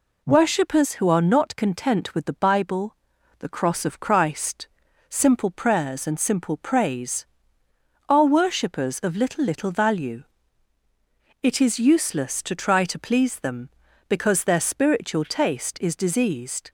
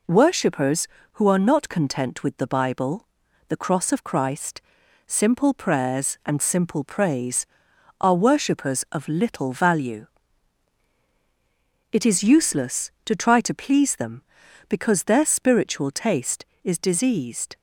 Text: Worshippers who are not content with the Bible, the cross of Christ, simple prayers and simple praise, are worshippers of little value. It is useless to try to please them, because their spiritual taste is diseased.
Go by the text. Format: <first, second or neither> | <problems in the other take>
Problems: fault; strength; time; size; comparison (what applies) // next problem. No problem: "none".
second | says "little" twice; at 9.4 s